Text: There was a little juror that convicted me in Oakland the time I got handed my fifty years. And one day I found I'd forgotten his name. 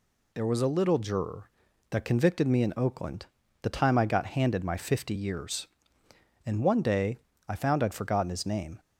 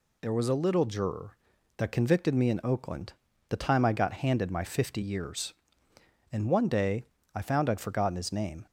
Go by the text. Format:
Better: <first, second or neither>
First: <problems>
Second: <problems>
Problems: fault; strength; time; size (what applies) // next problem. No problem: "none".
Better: neither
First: pauses between "Oakland" and "the"; slight; at 3.2 s; 0.36 s long // pauses between "day" and "I"; slight; at 7.1 s; 0.30 s long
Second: pauses between "Oakland" and "the"; slight; at 3.1 s; 0.36 s long // pauses between "day" and "I"; slight; at 7.0 s; 0.30 s long